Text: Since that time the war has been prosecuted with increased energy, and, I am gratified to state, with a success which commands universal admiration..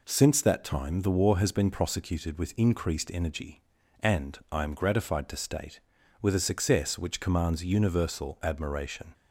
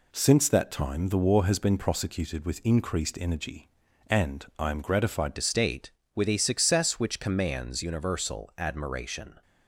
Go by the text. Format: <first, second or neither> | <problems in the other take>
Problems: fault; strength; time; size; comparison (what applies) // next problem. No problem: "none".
first | changes voice at "to"; from 5.3 s on; 4.1 s long